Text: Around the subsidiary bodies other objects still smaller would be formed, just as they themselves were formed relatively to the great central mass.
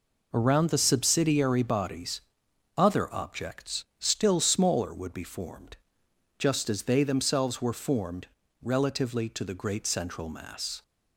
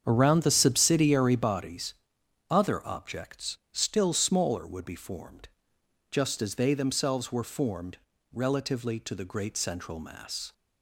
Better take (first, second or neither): first